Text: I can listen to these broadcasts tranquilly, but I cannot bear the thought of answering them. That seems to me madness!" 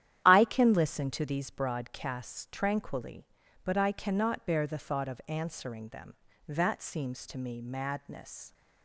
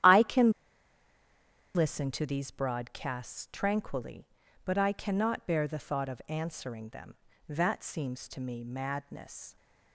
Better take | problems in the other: first | starts louder than the rest; strong; until 2.2 s; 11 dB; strong in the first // pauses between "can" and "listen"; strong; at 0.4 s; 1.2 s long

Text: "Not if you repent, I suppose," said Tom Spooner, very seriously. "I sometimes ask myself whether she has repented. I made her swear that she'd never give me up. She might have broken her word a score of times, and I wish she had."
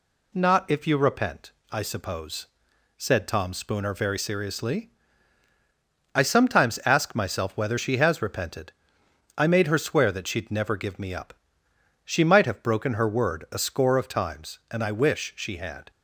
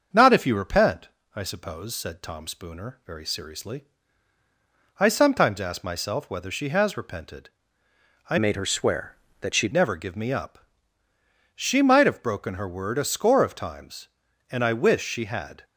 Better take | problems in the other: first | starts louder than the rest; until 1.3 s; 7 dB // changes voice from "made" to "she'd"; from 8.3 to 9.7 s; 1.4 s long

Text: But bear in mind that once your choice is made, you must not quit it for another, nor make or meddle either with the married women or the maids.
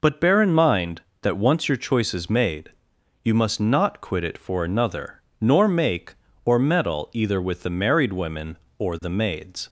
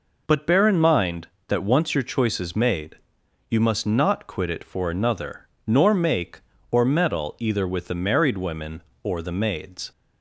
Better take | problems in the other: neither | none

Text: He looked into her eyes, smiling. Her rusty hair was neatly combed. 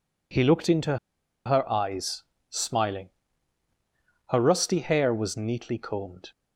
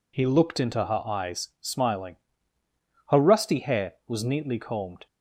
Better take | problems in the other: second | pauses between "into" and "her"; noticeable; at 0.9 s; 0.49 s long

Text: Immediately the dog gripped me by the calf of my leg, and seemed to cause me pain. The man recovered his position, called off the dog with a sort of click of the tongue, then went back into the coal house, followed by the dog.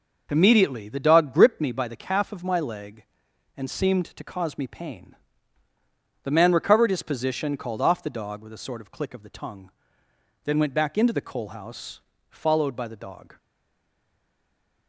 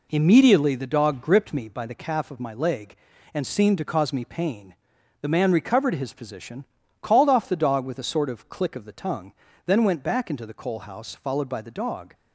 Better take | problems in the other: second | stays silent after the last word; noticeable; from 13.3 s on; 1.5 s long

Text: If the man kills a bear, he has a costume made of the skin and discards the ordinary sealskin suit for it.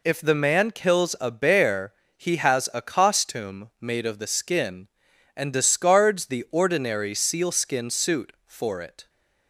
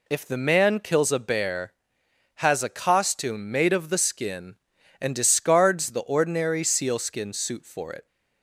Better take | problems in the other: first | skips "he"; at 2.0 s

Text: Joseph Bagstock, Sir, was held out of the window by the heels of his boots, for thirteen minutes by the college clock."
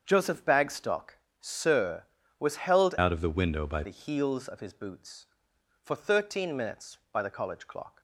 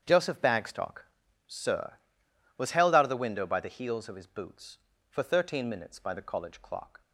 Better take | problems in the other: second | starts louder than the rest; strong; until 1.0 s; 7.5 dB; strong in the second // changes voice from "out" to "by"; from 2.9 to 3.8 s; 0.9 s long

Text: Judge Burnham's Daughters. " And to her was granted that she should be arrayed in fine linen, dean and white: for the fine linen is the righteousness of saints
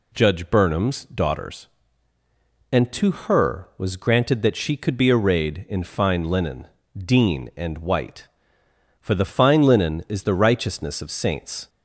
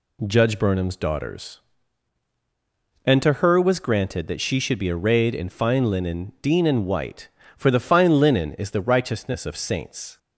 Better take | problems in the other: second | says "could" for "should"; at 4.7 s

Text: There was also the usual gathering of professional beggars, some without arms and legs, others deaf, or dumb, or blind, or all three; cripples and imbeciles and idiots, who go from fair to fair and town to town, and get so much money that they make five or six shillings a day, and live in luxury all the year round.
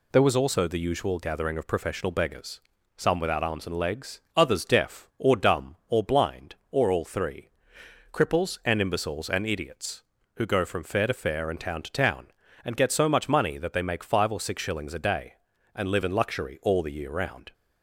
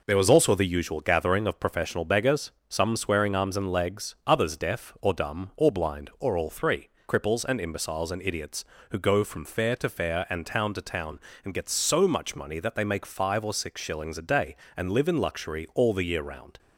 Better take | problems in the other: first | says "swearing" for "without"; at 2.9 s

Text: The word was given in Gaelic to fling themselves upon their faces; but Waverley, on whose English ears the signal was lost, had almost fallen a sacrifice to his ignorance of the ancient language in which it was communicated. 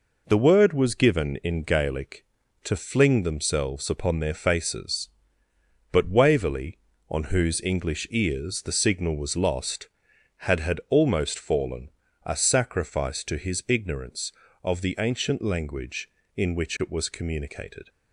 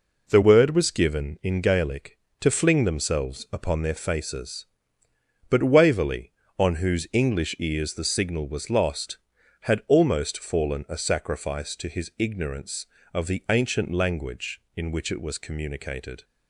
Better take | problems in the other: second | says "had" twice; at 10.5 s // pauses between "fallen" and "a"; slight; at 11.8 s; 0.34 s long

